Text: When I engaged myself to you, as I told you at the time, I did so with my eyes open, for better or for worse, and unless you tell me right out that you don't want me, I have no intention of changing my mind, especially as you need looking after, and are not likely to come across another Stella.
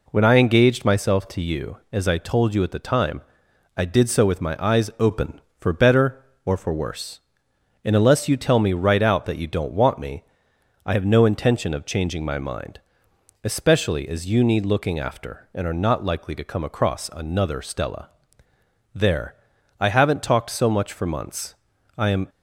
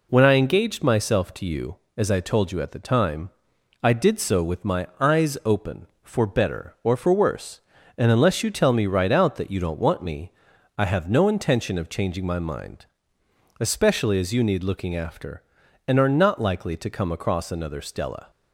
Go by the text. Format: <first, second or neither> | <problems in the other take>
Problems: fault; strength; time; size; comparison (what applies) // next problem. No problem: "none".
second | goes on to say "There I haven't talked so much for months I am"; strong; from 18.9 s on; 3.3 s long